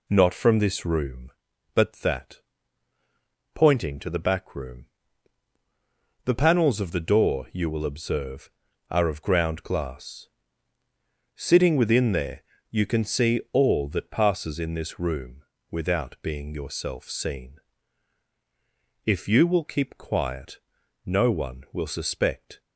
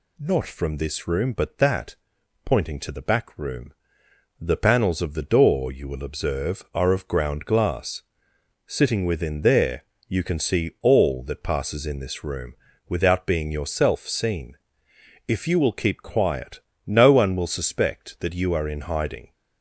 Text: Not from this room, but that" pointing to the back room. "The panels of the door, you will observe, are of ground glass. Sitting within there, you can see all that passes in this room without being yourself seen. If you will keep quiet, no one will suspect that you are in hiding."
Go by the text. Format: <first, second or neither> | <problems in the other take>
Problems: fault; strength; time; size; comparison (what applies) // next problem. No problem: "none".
second | pauses between "that" and "pointing"; at 2.3 s; 1.1 s long; noticeable in the second // pauses between "room" and "without"; slight; at 15.4 s; 0.28 s long; slight in the second // stops before "that you are in hiding"; at 22.6 s